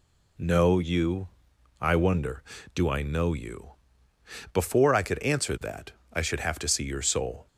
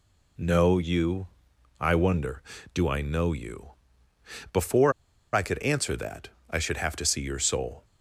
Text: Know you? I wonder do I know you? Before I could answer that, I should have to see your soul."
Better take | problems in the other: first | pauses between "Before" and "I"; at 4.9 s; 0.41 s long

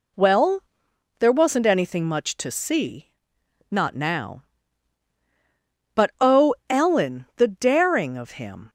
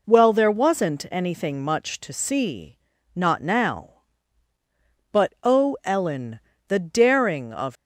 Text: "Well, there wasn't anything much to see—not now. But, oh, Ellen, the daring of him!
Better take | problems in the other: first | stops before "him"; at 7.7 s

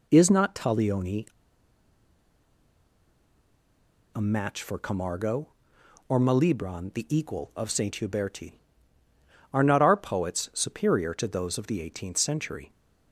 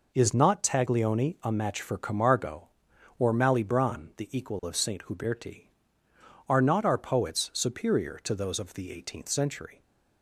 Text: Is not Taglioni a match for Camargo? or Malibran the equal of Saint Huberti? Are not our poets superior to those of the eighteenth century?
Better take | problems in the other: second | pauses between "Taglioni" and "a"; strong; at 1.2 s; 2.8 s long

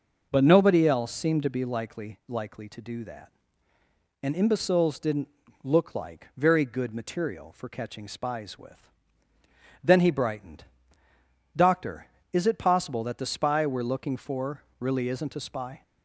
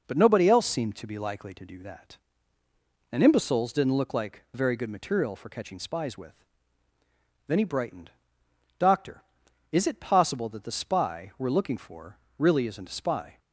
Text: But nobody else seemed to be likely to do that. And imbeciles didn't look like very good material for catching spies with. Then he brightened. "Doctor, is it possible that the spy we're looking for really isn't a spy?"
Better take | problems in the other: second | says "likely" twice; at 2.2 s // pauses between "didn't" and "look"; slight; at 5.2 s; 0.34 s long // pauses between "for" and "really"; slight; at 14.6 s; 0.18 s long; slight in the second

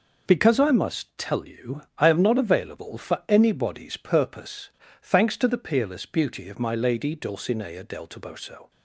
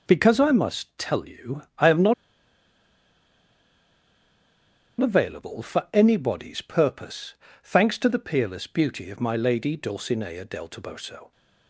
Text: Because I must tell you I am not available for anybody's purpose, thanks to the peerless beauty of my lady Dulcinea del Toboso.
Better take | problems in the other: first | pauses between "not" and "available"; strong; at 2.1 s; 2.8 s long

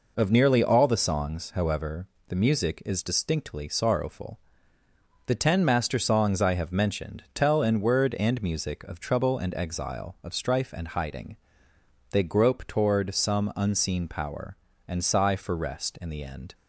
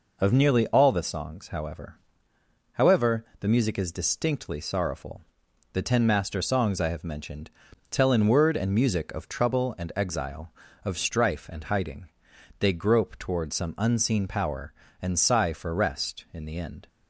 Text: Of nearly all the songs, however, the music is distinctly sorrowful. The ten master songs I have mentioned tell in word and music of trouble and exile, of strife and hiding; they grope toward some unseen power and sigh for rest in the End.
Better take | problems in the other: first | says "however" twice; at 2.7 s // pauses between "mentioned" and "tell"; at 7.4 s; 0.40 s long

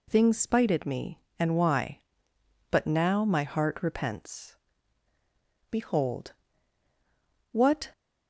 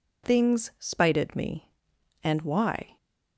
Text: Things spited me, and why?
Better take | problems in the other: second | goes on to say "But now my heart repents Behold What"; strong; from 2.7 s on; 5.2 s long

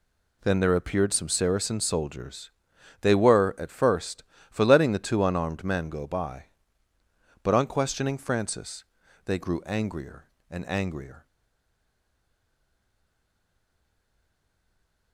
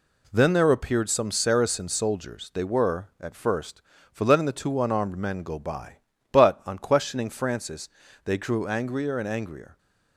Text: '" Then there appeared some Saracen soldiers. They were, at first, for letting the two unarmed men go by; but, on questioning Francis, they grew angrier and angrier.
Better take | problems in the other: second | stays silent after the last word; strong; from 11.2 s on; 3.9 s long

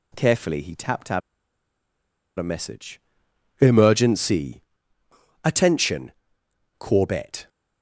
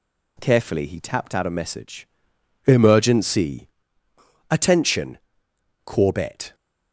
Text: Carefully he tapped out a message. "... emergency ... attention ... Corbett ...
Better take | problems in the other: second | pauses between "out" and "a"; at 1.2 s; 1.1 s long

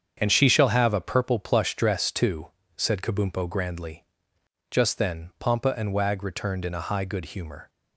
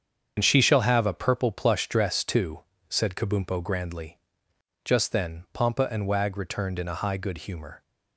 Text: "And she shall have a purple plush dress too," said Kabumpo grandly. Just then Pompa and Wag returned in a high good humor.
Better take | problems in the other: first | loses the start of "And"; at 0.3 s; 75 ms // starts louder than the rest; strong; until 1.3 s; 7.5 dB; strong in the first

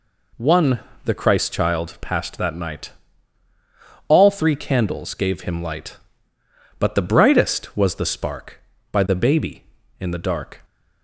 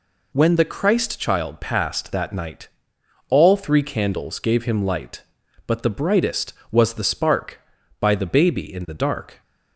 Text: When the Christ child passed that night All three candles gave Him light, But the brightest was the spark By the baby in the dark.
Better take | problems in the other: second | says "One" for "When"; at 0.3 s // pauses between "night" and "All"; at 2.9 s; 1.1 s long; noticeable in the second

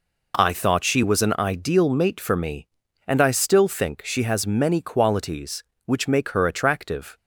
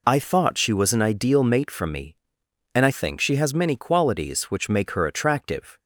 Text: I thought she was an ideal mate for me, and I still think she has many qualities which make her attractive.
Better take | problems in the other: first | skips "still"; at 2.9 s

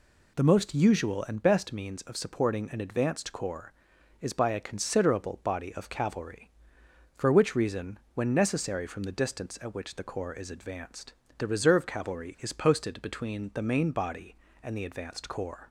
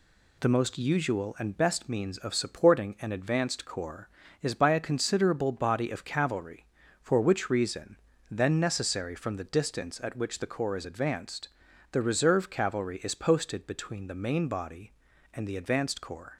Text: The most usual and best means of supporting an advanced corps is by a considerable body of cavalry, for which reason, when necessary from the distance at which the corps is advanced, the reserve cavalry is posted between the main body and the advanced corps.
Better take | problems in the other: first | says "then" for "when"; at 8.2 s

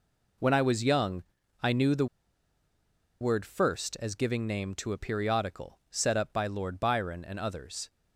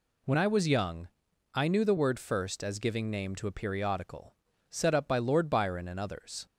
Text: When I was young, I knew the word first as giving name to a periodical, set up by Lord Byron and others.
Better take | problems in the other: second | pauses between "the" and "word"; at 2.0 s; 1.1 s long

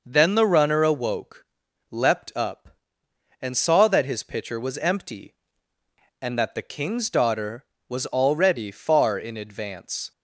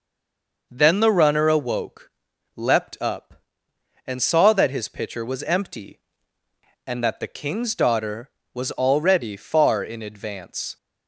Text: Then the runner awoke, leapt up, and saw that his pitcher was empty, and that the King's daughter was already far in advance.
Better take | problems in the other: first | stays silent before the first word; slight; until 0.7 s; 0.7 s long

